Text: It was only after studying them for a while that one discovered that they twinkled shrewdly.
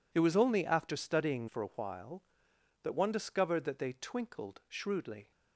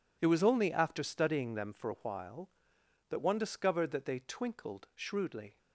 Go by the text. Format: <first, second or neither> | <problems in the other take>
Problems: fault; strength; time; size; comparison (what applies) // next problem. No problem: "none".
second | skips "them"; at 1.4 s